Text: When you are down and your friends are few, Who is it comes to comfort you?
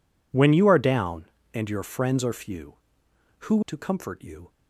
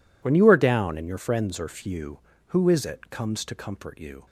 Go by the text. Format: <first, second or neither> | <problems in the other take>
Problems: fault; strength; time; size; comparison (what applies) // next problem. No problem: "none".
second | skips "is it comes"; at 3.6 s